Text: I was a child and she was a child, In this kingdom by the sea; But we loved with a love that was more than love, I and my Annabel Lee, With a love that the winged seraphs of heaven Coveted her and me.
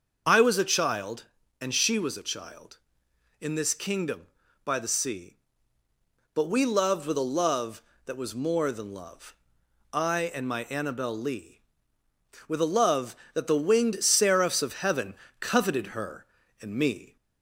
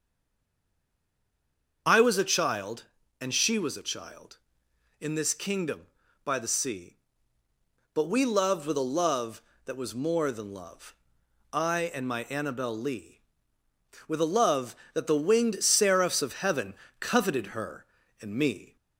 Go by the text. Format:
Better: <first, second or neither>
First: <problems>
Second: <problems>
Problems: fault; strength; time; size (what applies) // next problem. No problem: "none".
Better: first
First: starts louder than the rest; until 1.6 s; 6.5 dB // pauses between "heaven" and "Coveted"; slight; at 15.1 s; 0.26 s long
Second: stays silent before the first word; noticeable; until 1.8 s; 1.8 s long // starts louder than the rest; until 3.2 s; 6.5 dB // pauses between "heaven" and "Coveted"; slight; at 16.7 s; 0.26 s long